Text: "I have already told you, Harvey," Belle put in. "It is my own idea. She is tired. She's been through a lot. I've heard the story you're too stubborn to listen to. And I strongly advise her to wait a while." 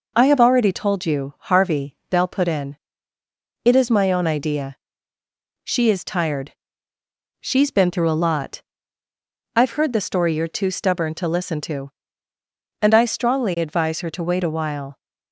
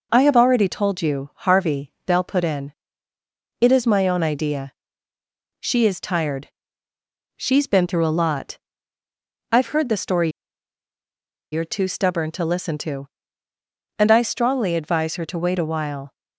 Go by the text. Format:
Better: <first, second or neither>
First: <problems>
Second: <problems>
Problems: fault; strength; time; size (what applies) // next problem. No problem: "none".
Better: first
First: none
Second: pauses between "story" and "you're"; at 10.3 s; 1.2 s long